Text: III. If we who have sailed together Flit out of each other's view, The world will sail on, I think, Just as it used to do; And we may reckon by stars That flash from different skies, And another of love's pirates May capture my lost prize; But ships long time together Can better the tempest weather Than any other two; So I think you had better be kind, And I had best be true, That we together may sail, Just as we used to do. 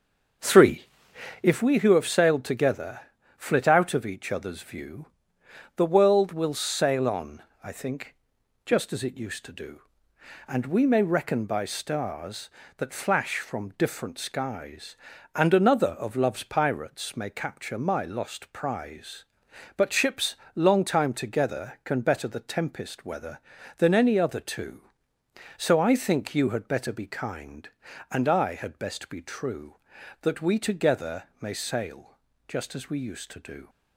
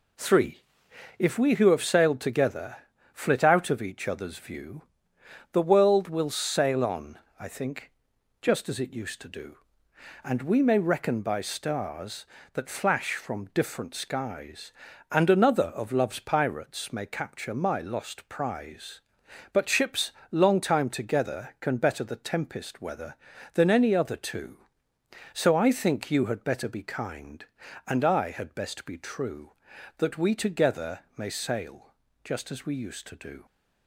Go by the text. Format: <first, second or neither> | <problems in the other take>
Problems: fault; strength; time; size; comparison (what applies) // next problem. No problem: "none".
second | starts louder than the rest; until 1.7 s; 6.5 dB // pauses between "together" and "Flit"; slight; at 3.0 s; 0.36 s long; slight in the second // pauses between "ships" and "long"; slight; at 20.3 s; 0.20 s long; slight in the second // pauses between "together" and "may"; slight; at 31.2 s; 0.18 s long; slight in the second